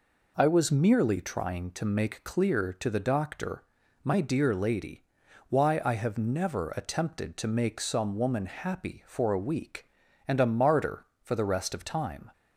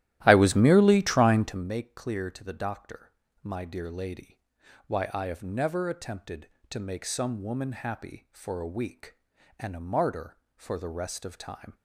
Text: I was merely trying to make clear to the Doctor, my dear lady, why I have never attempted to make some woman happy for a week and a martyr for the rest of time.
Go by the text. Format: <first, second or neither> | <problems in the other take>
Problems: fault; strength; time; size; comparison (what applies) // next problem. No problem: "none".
first | starts louder than the rest; strong; until 1.7 s; 14 dB